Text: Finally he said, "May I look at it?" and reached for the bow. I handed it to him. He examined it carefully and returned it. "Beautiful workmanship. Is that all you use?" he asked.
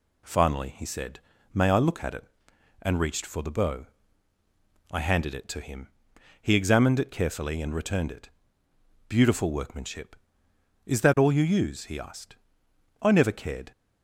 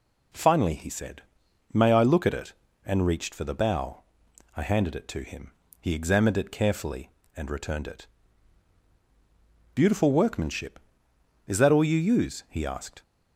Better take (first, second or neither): second